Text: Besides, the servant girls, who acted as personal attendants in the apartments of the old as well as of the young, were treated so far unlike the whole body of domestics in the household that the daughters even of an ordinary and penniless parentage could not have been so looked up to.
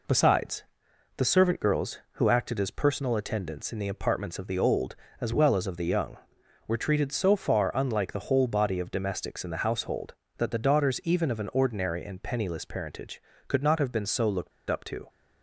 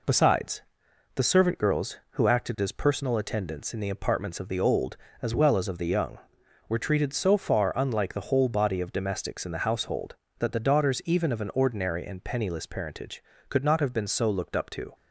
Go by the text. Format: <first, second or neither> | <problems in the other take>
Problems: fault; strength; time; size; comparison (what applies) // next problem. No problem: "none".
second | pauses between "looked" and "up"; slight; at 14.5 s; 0.18 s long